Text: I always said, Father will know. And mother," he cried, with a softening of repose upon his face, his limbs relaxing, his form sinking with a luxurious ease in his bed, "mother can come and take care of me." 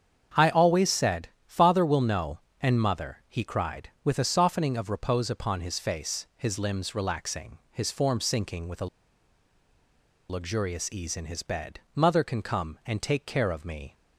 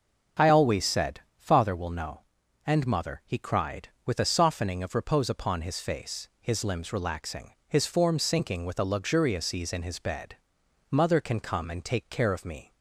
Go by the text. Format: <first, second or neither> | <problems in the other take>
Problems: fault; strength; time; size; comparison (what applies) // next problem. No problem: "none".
second | starts louder than the rest; strong; until 1.5 s; 7.5 dB; also in the second // pauses between "a" and "luxurious"; strong; at 8.8 s; 1.4 s long